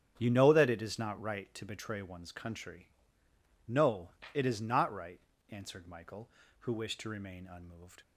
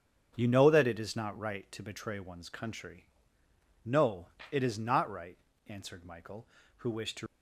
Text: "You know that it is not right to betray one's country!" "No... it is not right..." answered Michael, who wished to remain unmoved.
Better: first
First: starts louder than the rest; strong; until 1.1 s; 9 dB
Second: starts louder than the rest; strong; until 1.3 s; 8 dB // stops before "remain unmoved"; at 7.2 s

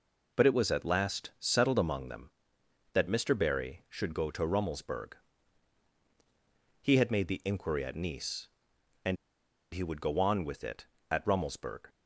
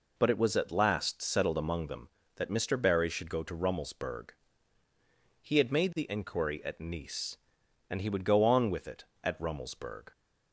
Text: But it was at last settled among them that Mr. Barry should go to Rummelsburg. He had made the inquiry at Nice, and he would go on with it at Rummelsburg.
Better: second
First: pauses between "and" and "he"; noticeable; at 9.1 s; 0.58 s long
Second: none

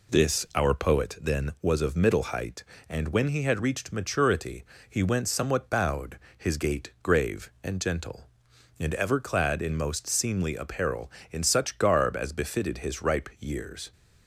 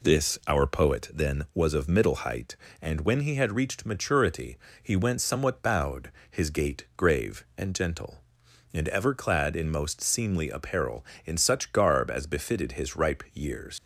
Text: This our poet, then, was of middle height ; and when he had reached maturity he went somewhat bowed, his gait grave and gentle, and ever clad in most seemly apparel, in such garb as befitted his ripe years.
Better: first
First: pauses between "maturity" and "he"; slight; at 4.6 s; 0.26 s long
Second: pauses between "maturity" and "he"; slight; at 4.5 s; 0.26 s long // leaves "years" unfinished; at 13.7 s; 75 ms

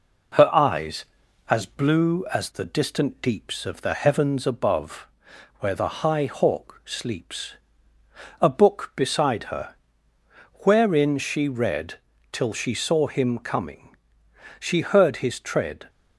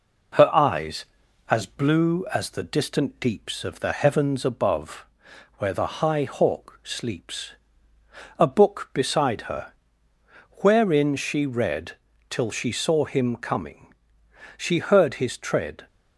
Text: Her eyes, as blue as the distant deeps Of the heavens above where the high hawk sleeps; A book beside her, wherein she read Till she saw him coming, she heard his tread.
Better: neither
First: pauses between "above" and "where"; noticeable; at 5.0 s; 0.54 s long // pauses between "read" and "Till"; slight; at 11.9 s; 0.34 s long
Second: pauses between "above" and "where"; noticeable; at 5.0 s; 0.54 s long // pauses between "read" and "Till"; slight; at 11.9 s; 0.34 s long

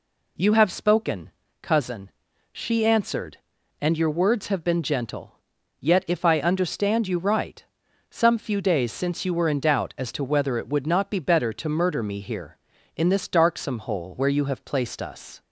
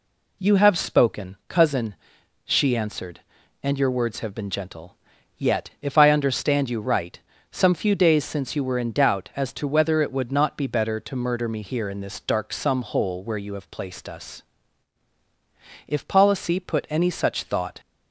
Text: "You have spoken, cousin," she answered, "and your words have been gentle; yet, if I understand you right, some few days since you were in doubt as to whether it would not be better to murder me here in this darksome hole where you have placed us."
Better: first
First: none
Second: goes on to say "If policy put any such thought"; strong; from 15.8 s on; 1.9 s long

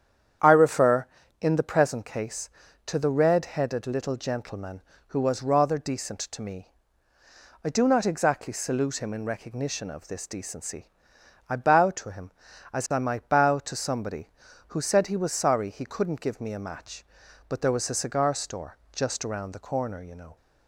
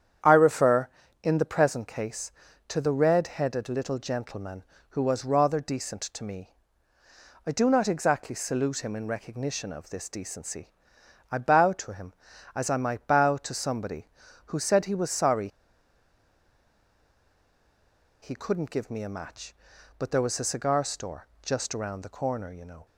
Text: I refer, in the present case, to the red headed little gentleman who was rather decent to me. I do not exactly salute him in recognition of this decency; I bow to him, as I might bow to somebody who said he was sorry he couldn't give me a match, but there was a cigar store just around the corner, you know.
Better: first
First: starts louder than the rest; strong; until 1.7 s; 9 dB // pauses between "store" and "just"; slight; at 18.7 s; 0.16 s long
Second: starts louder than the rest; strong; until 1.6 s; 9 dB // pauses between "sorry" and "he"; strong; at 15.4 s; 2.7 s long // pauses between "store" and "just"; slight; at 21.2 s; 0.16 s long

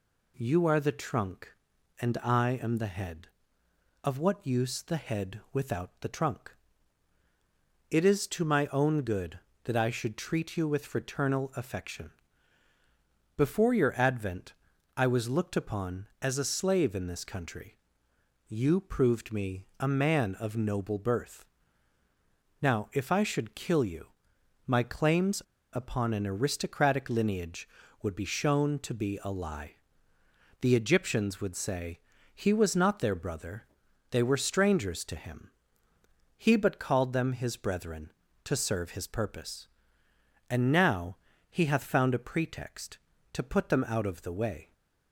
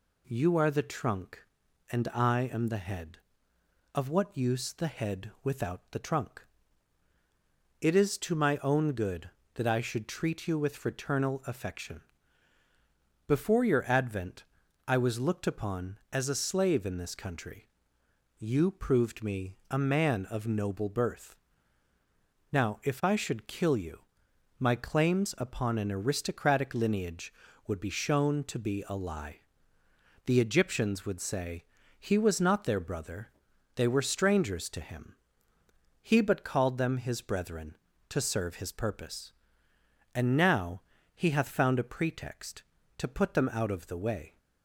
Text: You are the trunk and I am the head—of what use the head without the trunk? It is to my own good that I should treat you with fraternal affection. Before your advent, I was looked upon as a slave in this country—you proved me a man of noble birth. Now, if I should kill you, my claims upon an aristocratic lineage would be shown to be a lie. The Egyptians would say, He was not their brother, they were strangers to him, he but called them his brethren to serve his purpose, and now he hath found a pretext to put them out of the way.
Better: second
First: pauses between "claims" and "upon"; slight; at 25.4 s; 0.31 s long // pauses between "now" and "he"; slight; at 41.1 s; 0.32 s long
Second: pauses between "now" and "he"; slight; at 40.8 s; 0.32 s long

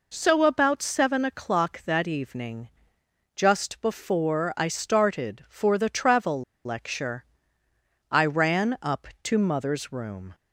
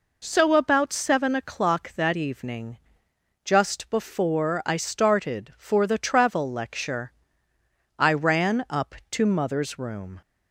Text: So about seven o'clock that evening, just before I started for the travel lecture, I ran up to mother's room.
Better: second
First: pauses between "travel" and "lecture"; slight; at 6.4 s; 0.22 s long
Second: none

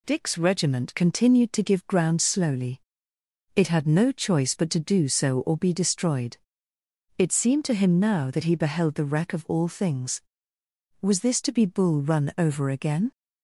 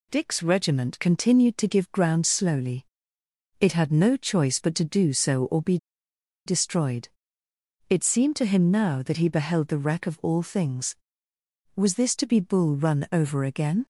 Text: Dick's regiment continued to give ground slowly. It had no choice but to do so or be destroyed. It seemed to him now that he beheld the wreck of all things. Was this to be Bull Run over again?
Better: first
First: none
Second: pauses between "be" and "destroyed"; noticeable; at 5.7 s; 0.69 s long

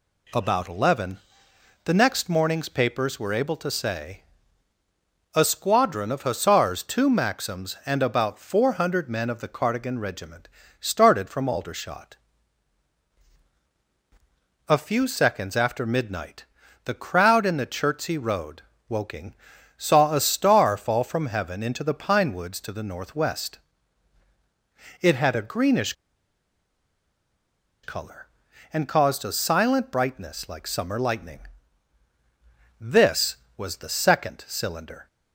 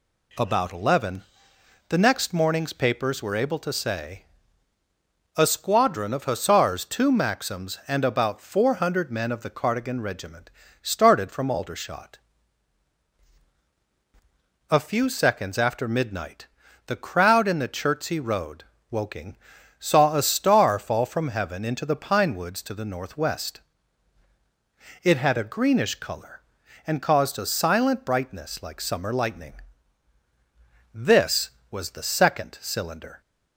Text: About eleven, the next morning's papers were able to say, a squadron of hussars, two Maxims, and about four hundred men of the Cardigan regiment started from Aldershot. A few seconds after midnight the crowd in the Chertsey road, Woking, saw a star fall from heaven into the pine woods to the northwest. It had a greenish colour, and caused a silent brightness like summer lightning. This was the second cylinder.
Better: second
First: pauses between "regiment" and "started"; slight; at 10.4 s; 0.32 s long // pauses between "midnight" and "the"; at 16.4 s; 0.40 s long // pauses between "greenish" and "colour"; strong; at 25.9 s; 1.9 s long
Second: pauses between "regiment" and "started"; slight; at 10.5 s; 0.32 s long // pauses between "midnight" and "the"; at 16.4 s; 0.40 s long

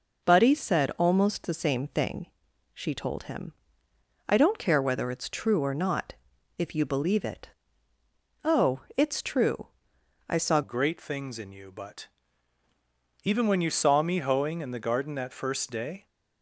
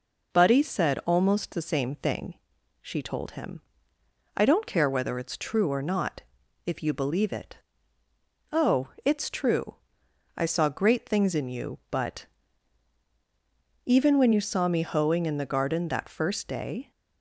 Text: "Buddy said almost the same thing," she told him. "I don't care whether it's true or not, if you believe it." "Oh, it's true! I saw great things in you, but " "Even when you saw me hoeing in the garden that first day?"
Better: second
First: changes voice at "great"; from 10.6 s on; 5.4 s long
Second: none

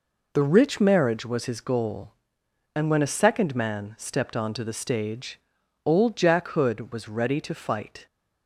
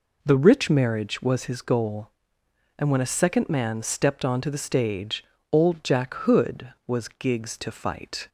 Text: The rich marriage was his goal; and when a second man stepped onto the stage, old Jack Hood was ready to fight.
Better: first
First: none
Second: says "gigs" for "ready"; at 7.0 s

